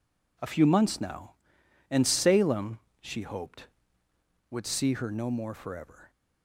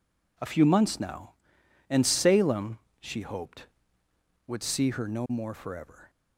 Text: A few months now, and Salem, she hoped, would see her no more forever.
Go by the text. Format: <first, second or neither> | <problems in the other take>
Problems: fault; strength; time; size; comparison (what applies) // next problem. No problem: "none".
neither | none